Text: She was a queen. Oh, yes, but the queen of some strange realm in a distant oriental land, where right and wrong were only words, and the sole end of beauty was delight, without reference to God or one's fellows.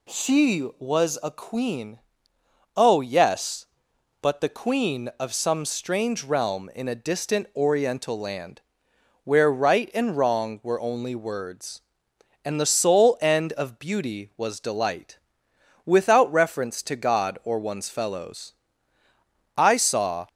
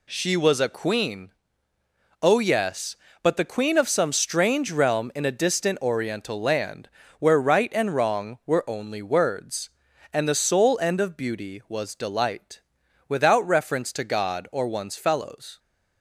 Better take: second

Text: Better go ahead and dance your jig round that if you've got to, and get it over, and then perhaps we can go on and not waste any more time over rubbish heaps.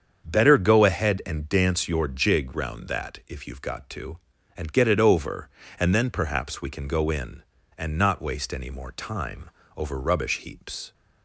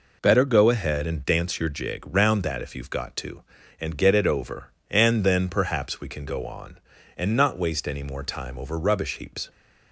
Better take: second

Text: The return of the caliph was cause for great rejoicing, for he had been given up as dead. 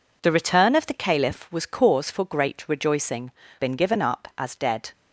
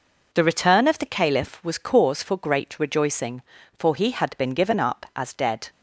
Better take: second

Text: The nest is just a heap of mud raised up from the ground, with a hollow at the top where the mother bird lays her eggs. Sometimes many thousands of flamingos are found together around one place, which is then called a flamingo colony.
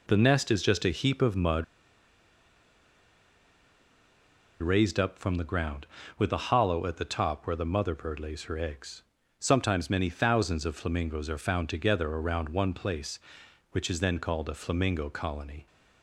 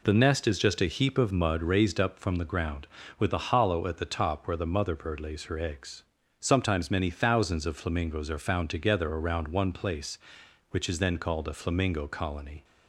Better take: second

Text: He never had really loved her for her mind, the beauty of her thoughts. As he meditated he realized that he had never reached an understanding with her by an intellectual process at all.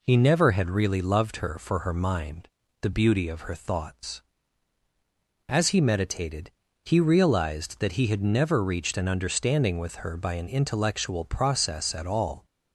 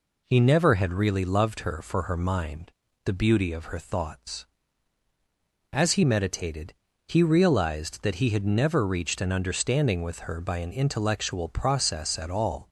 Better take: neither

